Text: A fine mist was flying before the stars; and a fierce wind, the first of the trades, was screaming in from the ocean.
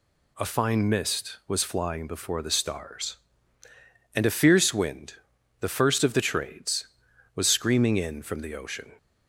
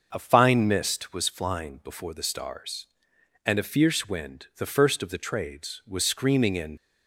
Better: first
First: none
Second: starts louder than the rest; until 1.1 s; 6 dB // stops before "from the ocean"; at 6.7 s

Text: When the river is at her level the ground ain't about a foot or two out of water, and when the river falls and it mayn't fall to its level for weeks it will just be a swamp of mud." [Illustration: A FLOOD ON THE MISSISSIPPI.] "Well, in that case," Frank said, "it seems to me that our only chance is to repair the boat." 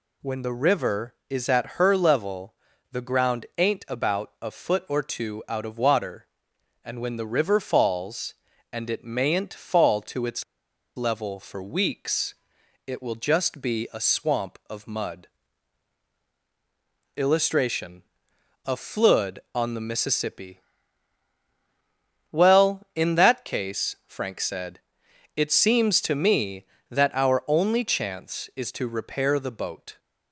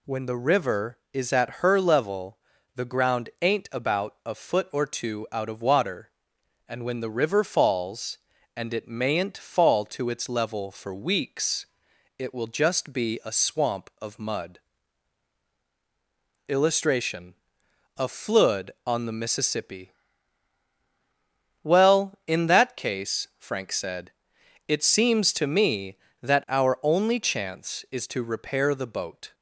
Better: second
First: pauses between "level" and "the"; at 2.5 s; 0.38 s long // pauses between "its" and "level"; noticeable; at 10.4 s; 0.52 s long // pauses between "weeks" and "it"; noticeable; at 12.3 s; 0.54 s long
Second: pauses between "level" and "the"; at 2.3 s; 0.38 s long // pauses between "weeks" and "it"; noticeable; at 11.6 s; 0.54 s long

